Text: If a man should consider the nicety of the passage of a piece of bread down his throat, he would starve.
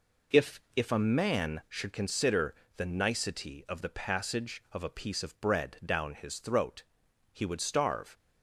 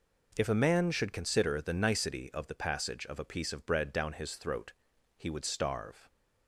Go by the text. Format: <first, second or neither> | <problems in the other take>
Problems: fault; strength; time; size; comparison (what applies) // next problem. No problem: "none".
second | says "If" twice; at 0.7 s // pauses between "consider" and "the"; slight; at 2.5 s; 0.22 s long